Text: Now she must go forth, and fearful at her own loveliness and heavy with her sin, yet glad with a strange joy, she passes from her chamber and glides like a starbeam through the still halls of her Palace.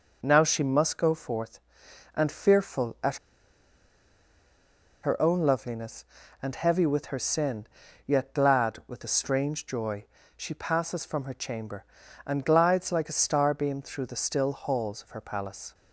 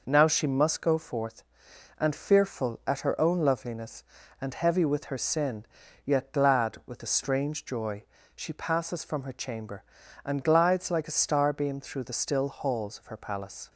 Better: second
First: pauses between "at" and "her"; strong; at 3.1 s; 1.8 s long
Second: none

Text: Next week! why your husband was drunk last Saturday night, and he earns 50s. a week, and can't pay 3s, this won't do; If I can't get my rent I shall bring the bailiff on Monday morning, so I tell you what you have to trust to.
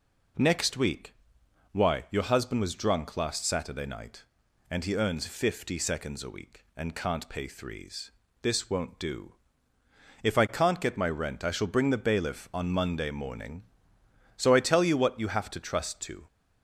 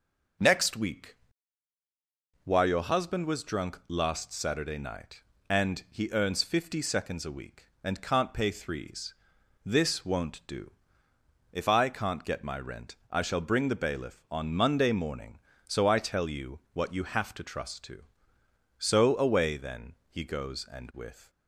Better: first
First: none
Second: starts louder than the rest; until 2.6 s; 6 dB // pauses between "rent" and "I"; slight; at 12.9 s; 0.16 s long // goes on to say "So away then he goes and with"; strong; from 18.7 s on; 2.5 s long

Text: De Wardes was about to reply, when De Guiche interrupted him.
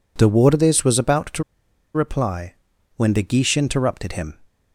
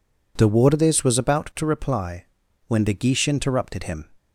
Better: second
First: pauses between "to" and "reply"; noticeable; at 1.4 s; 0.51 s long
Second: none

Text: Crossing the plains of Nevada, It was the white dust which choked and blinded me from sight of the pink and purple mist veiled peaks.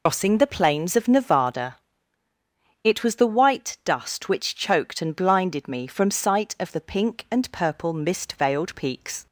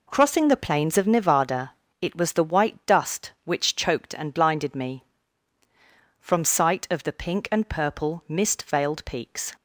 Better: second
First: loses the start of "Crossing"; at 0.0 s; 150 ms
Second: none

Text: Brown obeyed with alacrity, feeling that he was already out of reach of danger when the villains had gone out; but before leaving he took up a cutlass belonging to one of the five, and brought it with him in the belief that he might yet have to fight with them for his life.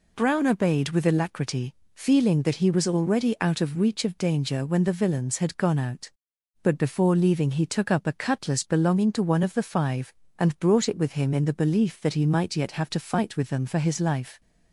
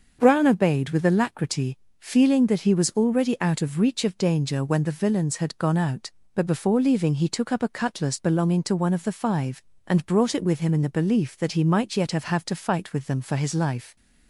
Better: first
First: none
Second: starts louder than the rest; until 1.2 s; 6.5 dB // says "have" twice; at 12.2 s

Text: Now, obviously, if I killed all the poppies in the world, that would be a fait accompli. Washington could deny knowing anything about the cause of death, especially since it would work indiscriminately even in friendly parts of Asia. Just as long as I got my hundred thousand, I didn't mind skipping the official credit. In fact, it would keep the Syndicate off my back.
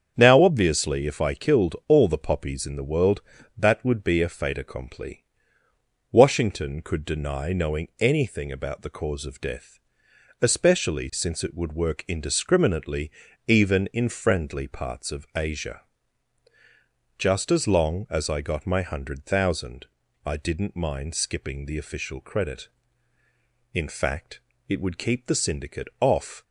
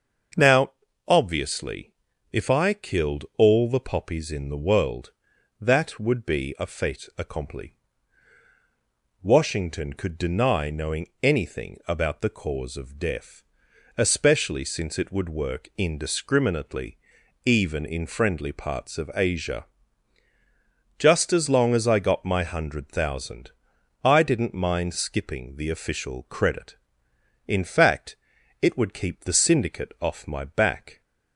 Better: second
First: starts louder than the rest; strong; until 1.1 s; 7.5 dB // pauses between "indiscriminately" and "even"; slight; at 13.1 s; 0.36 s long // stops before "my back"; at 26.4 s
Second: starts louder than the rest; until 1.7 s; 6.5 dB // pauses between "indiscriminately" and "even"; noticeable; at 16.9 s; 0.46 s long

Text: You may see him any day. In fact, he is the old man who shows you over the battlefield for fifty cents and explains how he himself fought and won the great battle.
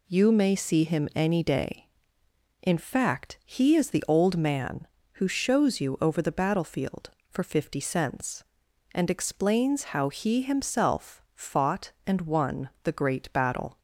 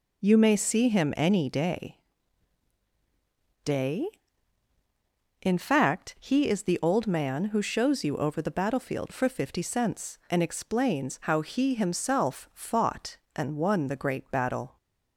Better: first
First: none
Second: says "day" twice; at 3.6 s

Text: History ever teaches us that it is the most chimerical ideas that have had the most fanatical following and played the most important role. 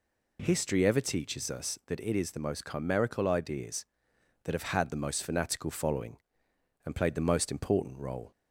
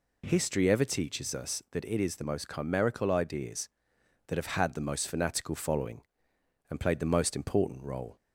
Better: neither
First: none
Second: none

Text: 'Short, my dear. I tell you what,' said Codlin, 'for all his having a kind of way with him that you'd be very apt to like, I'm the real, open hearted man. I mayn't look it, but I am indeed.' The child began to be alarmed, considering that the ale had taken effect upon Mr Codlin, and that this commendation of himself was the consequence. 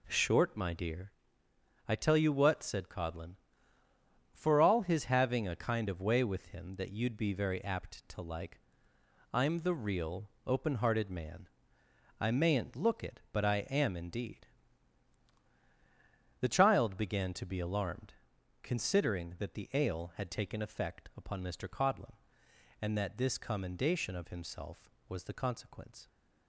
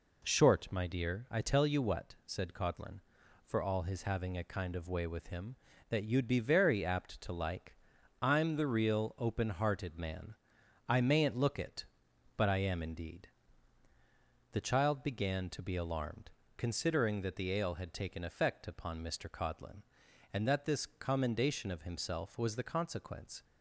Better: neither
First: none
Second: none

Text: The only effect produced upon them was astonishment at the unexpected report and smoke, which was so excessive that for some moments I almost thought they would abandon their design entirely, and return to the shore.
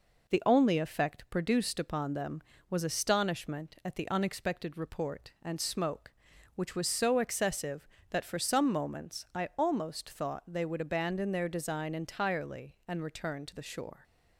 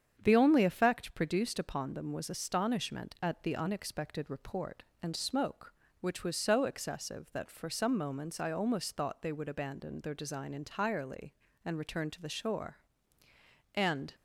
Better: first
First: none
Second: starts louder than the rest; strong; until 1.2 s; 8 dB // goes on to say "And"; slight; from 13.7 s on; 0.40 s long

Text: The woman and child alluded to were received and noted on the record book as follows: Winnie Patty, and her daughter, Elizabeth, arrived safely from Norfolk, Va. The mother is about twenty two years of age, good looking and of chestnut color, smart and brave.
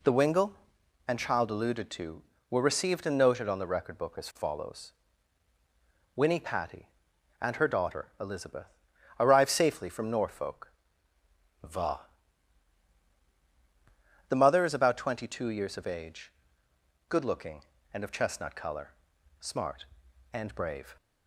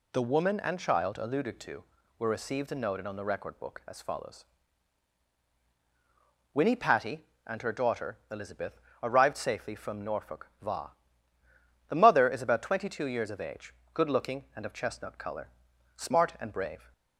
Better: second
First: says "wingle" for "woman"; at 0.1 s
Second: none

